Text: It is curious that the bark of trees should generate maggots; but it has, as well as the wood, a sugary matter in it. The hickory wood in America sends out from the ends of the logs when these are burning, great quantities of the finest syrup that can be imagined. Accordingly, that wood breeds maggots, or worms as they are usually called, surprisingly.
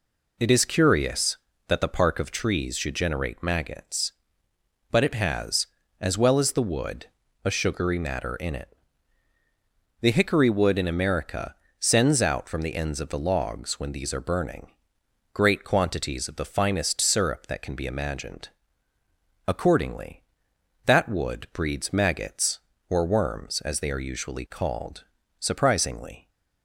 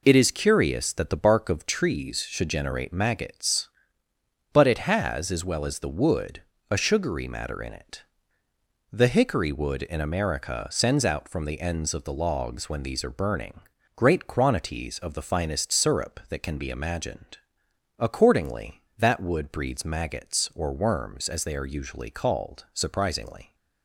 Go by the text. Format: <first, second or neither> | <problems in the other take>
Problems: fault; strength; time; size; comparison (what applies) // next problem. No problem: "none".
second | says "park" for "bark"; at 1.8 s // pauses between "America" and "sends"; slight; at 11.5 s; 0.24 s long